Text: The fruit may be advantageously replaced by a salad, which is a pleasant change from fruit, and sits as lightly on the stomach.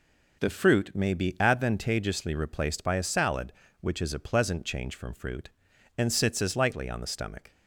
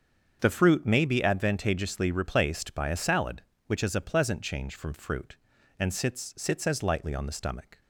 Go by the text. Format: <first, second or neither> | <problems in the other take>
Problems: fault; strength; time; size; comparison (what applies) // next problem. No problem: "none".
first | starts louder than the rest; until 1.4 s; 7 dB // says "sits" twice; at 6.3 s